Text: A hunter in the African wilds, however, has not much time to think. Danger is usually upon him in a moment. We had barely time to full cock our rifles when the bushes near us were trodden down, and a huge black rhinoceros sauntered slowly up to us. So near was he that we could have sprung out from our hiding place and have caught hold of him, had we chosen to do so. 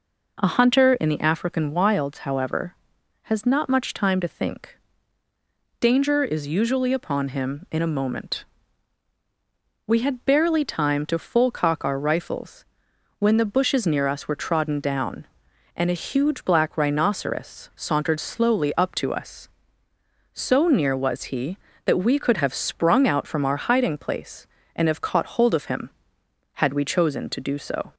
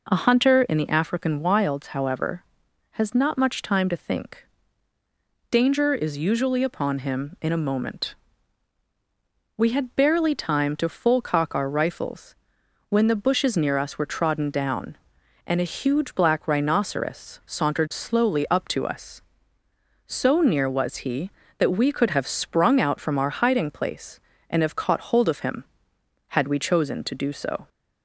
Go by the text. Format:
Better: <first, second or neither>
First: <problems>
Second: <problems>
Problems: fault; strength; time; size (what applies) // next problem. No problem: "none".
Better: neither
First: pauses between "rifles" and "when"; noticeable; at 12.6 s; 0.52 s long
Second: pauses between "rifles" and "when"; noticeable; at 12.3 s; 0.52 s long